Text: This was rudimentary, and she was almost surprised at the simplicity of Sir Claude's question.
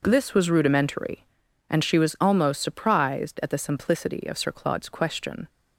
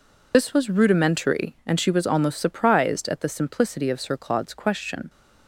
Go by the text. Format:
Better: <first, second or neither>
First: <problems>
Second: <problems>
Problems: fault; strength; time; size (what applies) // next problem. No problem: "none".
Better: first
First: none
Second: loses the start of "This"; at 0.3 s; 50 ms